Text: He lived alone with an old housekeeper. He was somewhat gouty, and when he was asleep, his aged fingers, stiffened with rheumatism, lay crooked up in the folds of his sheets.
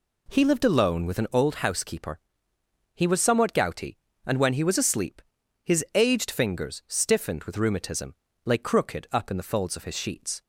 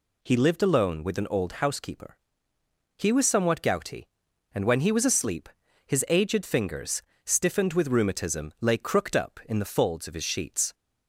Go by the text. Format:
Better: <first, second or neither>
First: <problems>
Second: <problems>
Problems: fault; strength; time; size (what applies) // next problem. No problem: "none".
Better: neither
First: none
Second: none